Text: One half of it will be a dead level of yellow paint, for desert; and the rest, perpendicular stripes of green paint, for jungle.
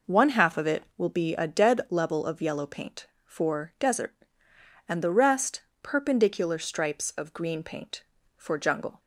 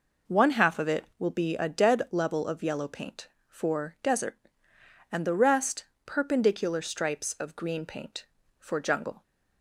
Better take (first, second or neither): neither